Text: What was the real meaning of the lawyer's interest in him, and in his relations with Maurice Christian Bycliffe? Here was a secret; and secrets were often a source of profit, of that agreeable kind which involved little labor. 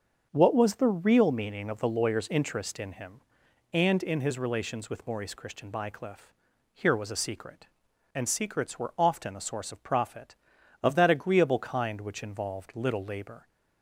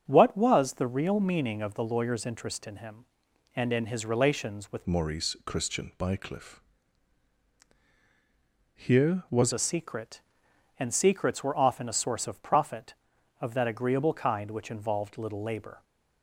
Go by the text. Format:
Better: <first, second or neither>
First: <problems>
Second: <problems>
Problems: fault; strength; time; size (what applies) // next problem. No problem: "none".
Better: first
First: starts louder than the rest; until 1.3 s; 7 dB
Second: starts louder than the rest; strong; until 1.0 s; 7.5 dB // changes voice from "Maurice" to "was"; from 4.8 to 9.5 s; 4.7 s long